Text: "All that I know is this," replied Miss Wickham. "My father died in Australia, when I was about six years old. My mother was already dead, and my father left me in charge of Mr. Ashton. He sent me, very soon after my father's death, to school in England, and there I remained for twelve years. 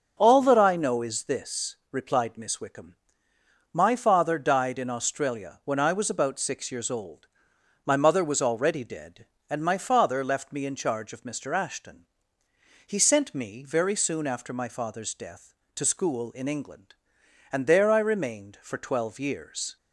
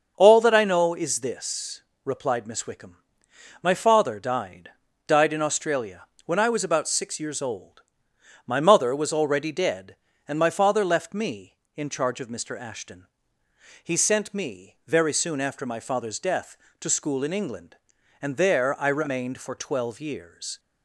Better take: first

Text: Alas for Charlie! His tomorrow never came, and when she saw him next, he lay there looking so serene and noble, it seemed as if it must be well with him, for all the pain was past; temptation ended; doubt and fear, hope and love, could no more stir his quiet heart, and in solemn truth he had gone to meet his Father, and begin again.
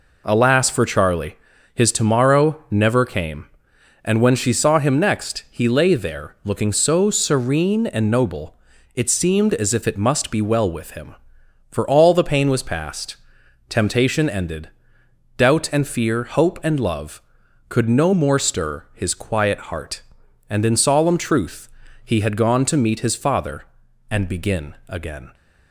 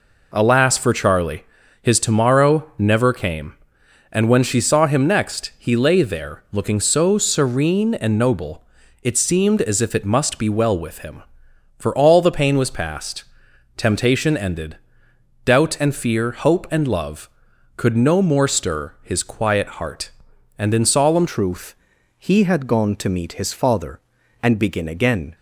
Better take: first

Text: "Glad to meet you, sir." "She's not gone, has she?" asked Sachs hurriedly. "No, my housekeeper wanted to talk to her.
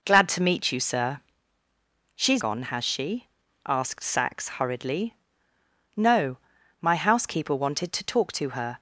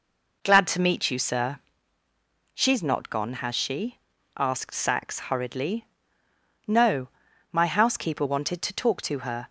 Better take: second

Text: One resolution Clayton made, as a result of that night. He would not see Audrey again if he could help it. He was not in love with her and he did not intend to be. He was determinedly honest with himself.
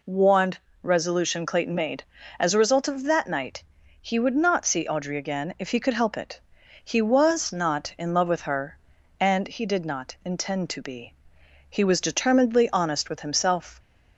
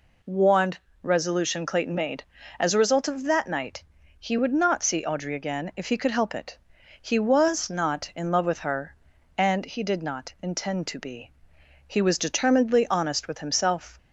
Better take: neither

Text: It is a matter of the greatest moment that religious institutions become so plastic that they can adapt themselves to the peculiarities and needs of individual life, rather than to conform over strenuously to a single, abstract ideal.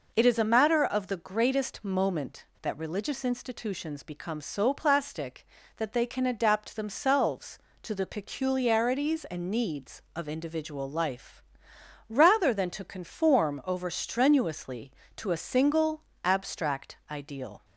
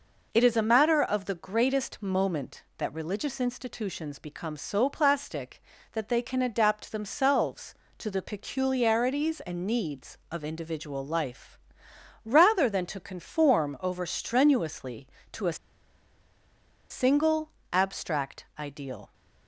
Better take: first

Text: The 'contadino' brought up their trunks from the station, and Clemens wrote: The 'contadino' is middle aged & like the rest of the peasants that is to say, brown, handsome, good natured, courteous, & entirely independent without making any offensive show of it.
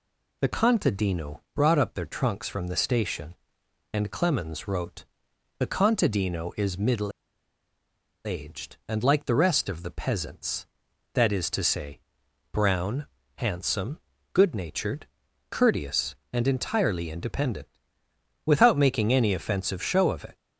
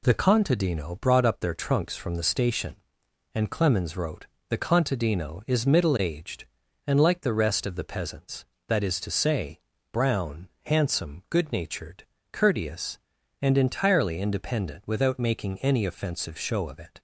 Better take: second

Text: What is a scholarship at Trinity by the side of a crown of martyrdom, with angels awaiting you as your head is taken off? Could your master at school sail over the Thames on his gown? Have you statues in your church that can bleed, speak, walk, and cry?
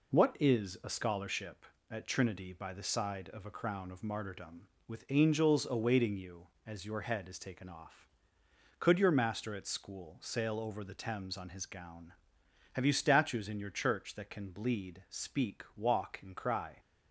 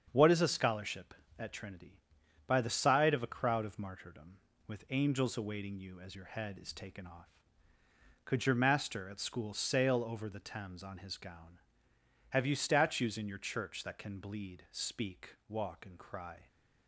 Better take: first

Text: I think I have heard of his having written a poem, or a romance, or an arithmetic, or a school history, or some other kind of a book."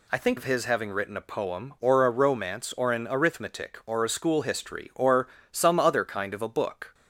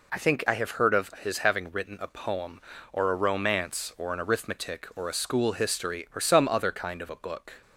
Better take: second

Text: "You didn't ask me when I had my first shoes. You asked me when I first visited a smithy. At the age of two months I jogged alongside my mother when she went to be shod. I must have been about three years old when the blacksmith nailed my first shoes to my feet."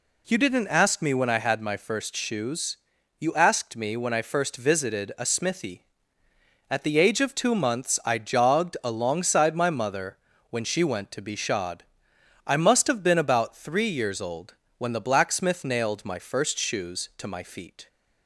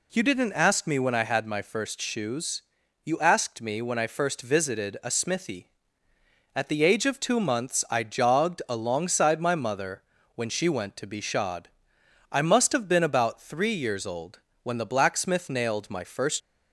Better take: first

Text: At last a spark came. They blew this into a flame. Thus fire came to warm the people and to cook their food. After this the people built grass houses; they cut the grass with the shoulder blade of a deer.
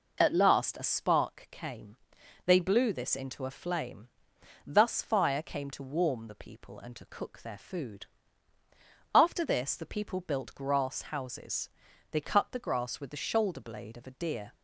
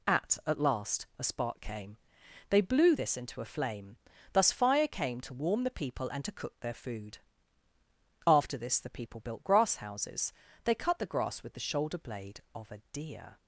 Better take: first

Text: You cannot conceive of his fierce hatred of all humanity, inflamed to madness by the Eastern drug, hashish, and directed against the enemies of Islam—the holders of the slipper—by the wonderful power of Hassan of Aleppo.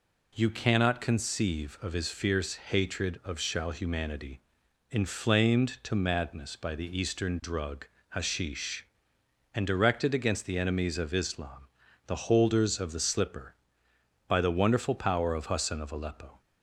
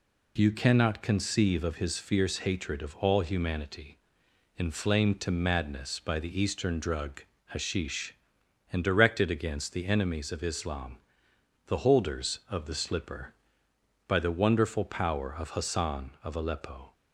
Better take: second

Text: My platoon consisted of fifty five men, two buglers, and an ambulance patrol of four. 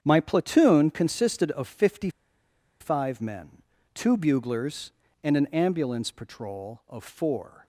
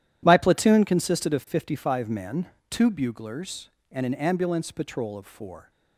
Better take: second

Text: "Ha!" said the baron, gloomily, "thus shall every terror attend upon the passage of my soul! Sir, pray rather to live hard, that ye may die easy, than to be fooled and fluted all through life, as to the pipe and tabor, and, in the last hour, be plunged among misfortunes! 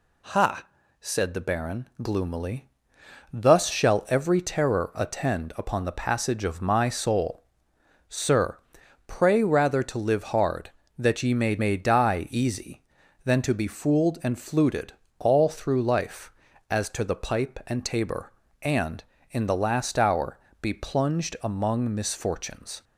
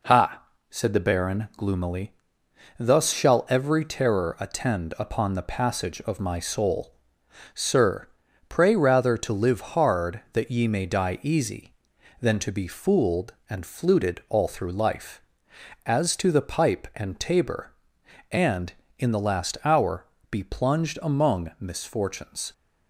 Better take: second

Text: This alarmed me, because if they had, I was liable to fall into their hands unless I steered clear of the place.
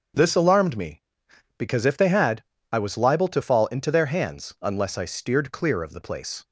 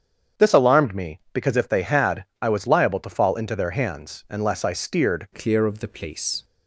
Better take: first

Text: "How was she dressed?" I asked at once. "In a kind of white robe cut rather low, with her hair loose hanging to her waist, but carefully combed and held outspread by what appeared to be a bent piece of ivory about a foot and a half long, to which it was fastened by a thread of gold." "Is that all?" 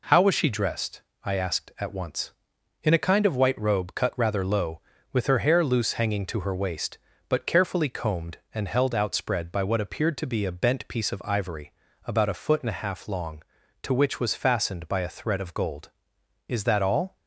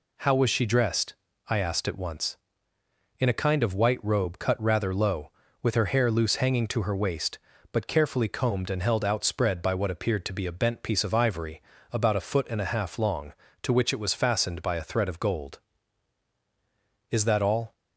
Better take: second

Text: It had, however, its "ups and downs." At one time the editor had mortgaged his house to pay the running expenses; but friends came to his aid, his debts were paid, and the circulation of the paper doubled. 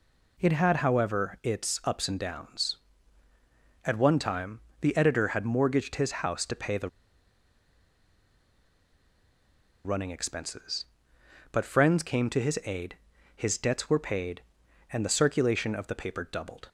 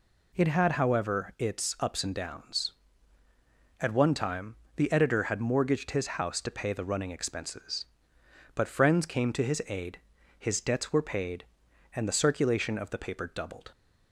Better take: second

